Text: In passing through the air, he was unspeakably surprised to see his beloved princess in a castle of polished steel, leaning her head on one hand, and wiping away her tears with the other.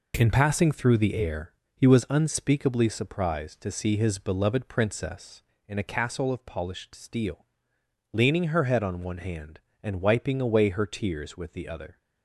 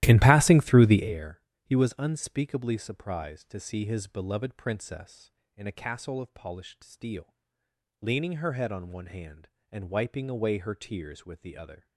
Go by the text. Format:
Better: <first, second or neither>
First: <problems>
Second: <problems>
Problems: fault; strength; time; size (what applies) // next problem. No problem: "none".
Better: first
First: none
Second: starts louder than the rest; strong; until 1.1 s; 14.5 dB